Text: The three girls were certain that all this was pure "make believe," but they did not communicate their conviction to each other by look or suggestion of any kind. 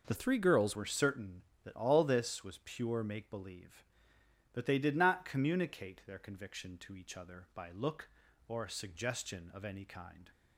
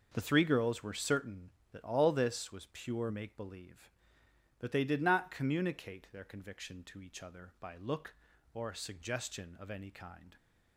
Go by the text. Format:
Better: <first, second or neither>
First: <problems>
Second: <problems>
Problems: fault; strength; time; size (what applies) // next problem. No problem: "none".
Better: second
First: changes voice from "three" to "girls"; from 0.1 to 0.7 s; 0.6 s long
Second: none